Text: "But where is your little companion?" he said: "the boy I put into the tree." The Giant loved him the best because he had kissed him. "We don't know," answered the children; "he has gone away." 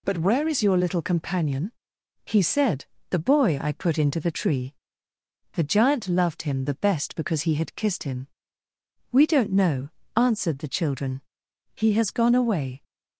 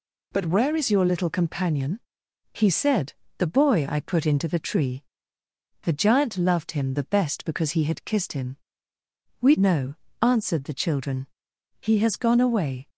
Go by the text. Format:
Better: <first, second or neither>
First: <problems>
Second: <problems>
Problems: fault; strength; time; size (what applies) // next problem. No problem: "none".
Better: first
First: none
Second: skips "don't"; at 9.5 s